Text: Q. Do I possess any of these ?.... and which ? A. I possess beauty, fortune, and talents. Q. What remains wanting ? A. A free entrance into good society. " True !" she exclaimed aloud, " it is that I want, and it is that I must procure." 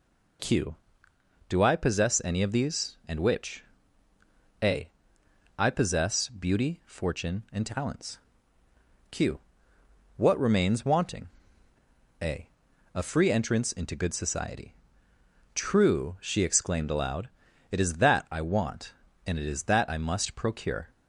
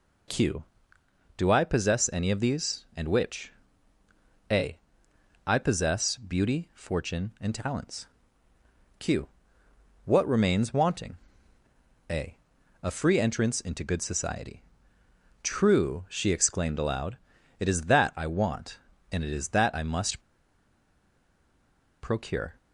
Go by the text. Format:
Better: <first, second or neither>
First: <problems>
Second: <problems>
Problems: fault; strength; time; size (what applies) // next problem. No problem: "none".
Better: first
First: none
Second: pauses between "must" and "procure"; strong; at 20.2 s; 1.8 s long